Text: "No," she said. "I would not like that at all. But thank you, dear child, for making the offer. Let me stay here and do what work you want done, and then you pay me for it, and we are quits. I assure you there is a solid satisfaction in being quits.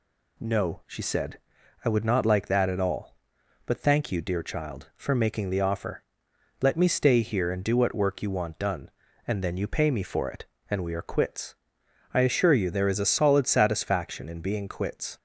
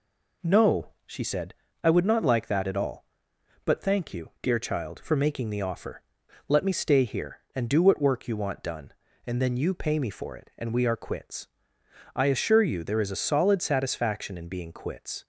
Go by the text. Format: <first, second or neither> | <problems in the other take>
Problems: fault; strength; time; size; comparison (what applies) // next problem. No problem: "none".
neither | none